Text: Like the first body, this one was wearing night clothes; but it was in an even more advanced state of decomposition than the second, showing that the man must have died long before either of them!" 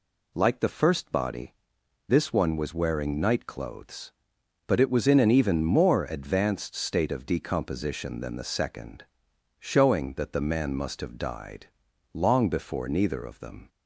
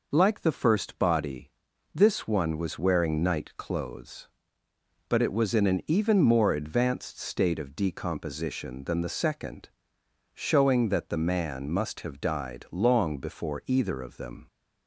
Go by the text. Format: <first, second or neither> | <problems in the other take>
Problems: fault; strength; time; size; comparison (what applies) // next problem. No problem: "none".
second | pauses between "died" and "long"; noticeable; at 11.6 s; 0.48 s long // says "neither" for "either"; at 12.8 s